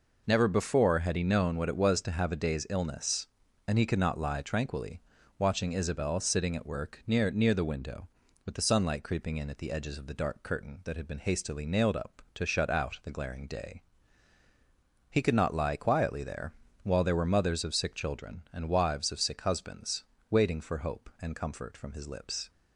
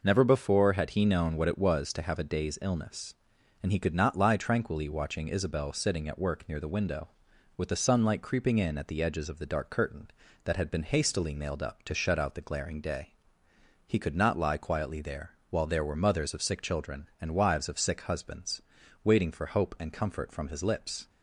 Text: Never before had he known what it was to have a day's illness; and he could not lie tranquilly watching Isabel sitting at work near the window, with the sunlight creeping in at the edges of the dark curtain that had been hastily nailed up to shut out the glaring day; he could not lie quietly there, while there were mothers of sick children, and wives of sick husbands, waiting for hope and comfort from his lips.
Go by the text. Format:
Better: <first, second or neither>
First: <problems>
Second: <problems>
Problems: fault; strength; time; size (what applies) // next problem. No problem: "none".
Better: second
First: pauses between "tranquilly" and "watching"; slight; at 5.0 s; 0.36 s long // says "near" twice; at 7.2 s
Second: none